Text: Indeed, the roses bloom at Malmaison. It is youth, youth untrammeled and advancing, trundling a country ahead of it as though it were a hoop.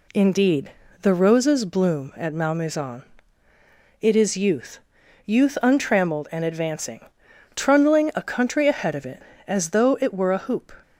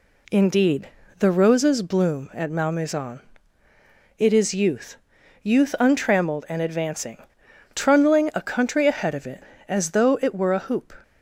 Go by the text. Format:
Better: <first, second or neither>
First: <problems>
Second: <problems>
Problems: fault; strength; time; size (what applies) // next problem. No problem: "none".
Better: neither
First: none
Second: none